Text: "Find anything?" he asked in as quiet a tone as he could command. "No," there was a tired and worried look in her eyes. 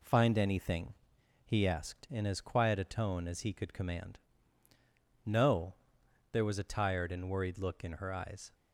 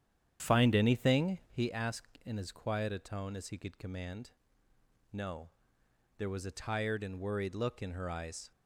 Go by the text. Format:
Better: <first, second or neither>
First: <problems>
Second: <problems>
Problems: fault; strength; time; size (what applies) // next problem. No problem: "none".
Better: first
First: none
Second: starts louder than the rest; strong; until 1.6 s; 9.5 dB